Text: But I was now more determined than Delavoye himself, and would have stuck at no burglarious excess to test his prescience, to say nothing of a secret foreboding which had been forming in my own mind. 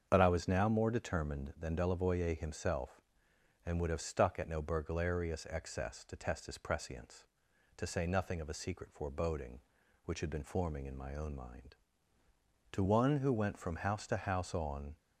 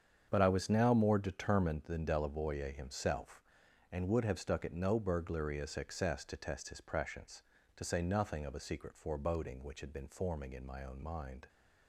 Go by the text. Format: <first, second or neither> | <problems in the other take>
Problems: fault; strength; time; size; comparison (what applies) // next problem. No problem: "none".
second | starts louder than the rest; until 1.1 s; 6.5 dB; strong in the second // goes on to say "To one who went from house to house on"; strong; from 12.7 s on; 2.2 s long